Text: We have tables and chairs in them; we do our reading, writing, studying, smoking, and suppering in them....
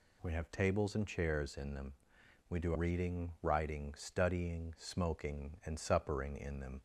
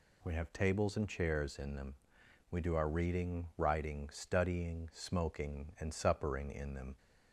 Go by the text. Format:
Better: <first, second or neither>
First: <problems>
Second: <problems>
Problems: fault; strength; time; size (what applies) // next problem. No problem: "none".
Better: second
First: skips "our"; at 2.7 s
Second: none